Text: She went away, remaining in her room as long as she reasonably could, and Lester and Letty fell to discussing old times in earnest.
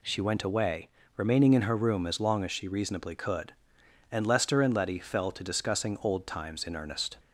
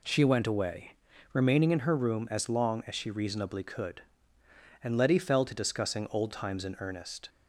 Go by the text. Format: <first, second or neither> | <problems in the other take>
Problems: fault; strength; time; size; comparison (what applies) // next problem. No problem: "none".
first | skips "Lester and"; at 4.9 s